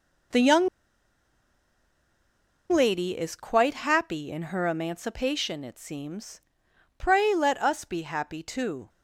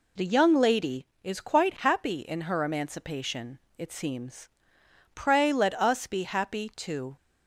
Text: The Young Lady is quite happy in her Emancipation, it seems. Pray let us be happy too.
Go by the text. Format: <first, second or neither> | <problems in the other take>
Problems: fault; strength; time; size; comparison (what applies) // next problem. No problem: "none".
second | pauses between "Young" and "Lady"; strong; at 0.6 s; 2.0 s long